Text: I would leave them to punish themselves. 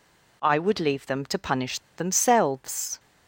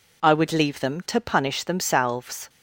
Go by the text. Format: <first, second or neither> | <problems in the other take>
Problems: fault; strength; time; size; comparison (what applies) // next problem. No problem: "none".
second | pauses between "punish" and "themselves"; slight; at 1.7 s; 0.18 s long